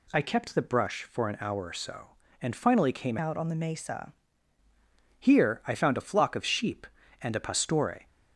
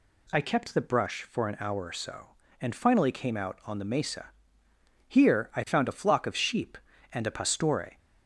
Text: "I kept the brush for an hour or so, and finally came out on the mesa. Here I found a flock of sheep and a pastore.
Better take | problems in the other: second | changes voice from "out" to "mesa"; from 3.1 to 4.1 s; 1.0 s long

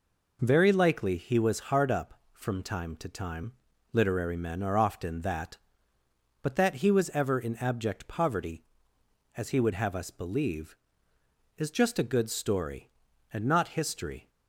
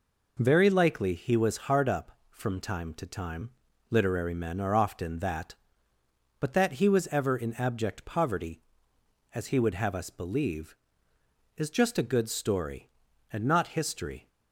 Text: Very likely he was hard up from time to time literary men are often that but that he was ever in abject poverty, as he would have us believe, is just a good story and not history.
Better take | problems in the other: neither | pauses between "time" and "literary"; the same in both

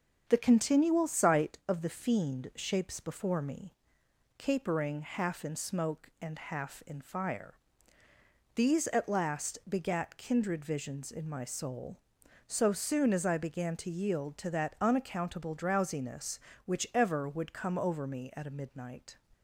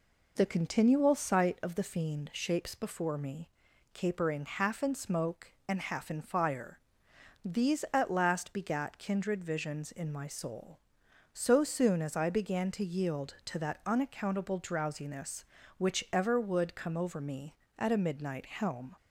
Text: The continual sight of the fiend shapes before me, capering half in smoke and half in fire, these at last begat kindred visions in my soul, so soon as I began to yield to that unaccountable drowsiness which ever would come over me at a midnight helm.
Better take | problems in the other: second | starts louder than the rest; until 1.2 s; 7 dB // stops before "helm"; at 19.3 s

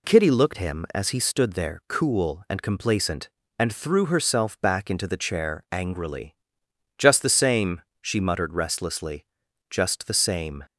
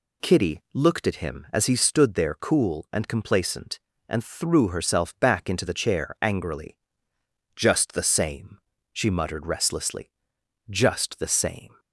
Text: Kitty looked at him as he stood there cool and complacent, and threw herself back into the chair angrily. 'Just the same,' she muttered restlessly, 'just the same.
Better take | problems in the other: second | skips "at"; at 0.5 s

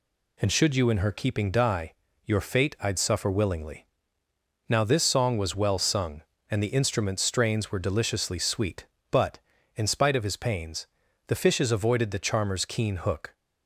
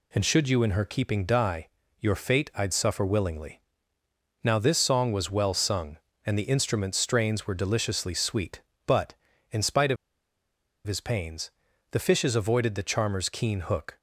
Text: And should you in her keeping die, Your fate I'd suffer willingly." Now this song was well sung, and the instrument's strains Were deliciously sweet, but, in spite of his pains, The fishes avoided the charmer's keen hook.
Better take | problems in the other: first | pauses between "of" and "his"; noticeable; at 9.9 s; 0.91 s long

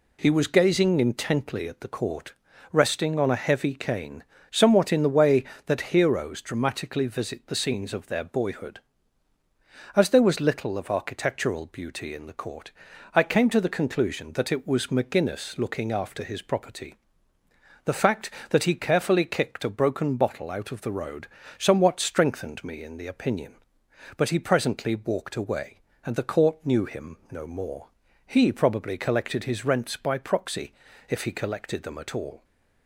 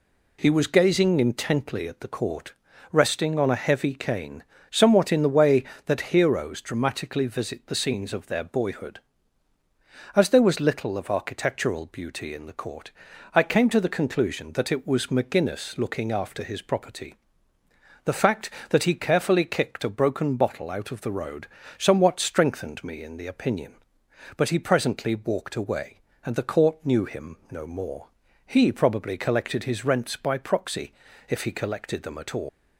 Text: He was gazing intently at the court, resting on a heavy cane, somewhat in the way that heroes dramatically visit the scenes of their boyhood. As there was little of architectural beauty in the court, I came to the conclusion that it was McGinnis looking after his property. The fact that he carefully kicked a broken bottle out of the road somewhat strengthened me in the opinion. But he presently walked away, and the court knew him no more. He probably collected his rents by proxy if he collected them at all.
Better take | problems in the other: first | pauses between "road" and "somewhat"; slight; at 21.4 s; 0.30 s long; slight in the first // pauses between "him" and "no"; slight; at 27.3 s; 0.16 s long; slight in the first // pauses between "proxy" and "if"; slight; at 30.9 s; 0.36 s long; slight in the first // leaves "all" unfinished; at 32.4 s; 140 ms

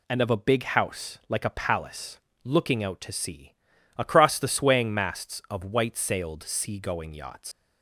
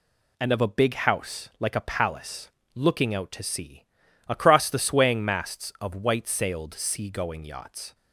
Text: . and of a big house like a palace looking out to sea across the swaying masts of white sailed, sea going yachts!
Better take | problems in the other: second | pauses between "palace" and "looking"; slight; at 2.1 s; 0.24 s long; slight in the second // pauses between "sea" and "across"; at 3.5 s; 0.42 s long; also in the second // leaves "yachts" unfinished; at 7.5 s; 125 ms

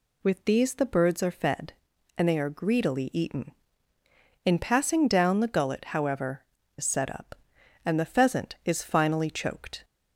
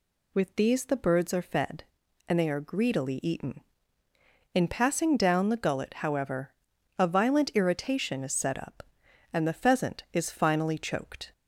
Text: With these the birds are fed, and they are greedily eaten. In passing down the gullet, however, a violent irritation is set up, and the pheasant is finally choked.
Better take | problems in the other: second | skips "a violent irritation"; at 6.6 s

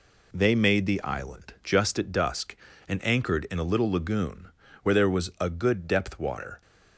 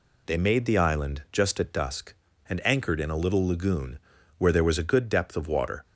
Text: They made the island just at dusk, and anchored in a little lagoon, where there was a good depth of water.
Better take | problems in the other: second | skips "of"; at 6.1 s

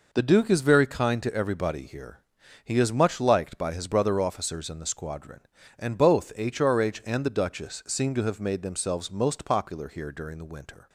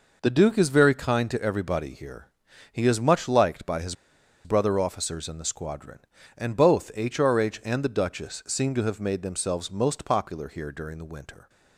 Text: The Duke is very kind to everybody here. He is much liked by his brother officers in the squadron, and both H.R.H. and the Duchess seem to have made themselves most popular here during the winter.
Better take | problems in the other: first | pauses between "his" and "brother"; noticeable; at 3.9 s; 0.51 s long

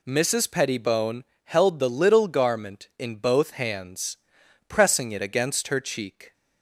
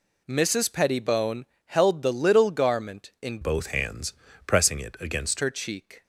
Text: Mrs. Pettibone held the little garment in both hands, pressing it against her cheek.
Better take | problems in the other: first | pauses between "Pettibone" and "held"; slight; at 1.4 s; 0.20 s long; slight in the first // changes voice from "both" to "against"; from 3.4 to 5.4 s; 2.0 s long

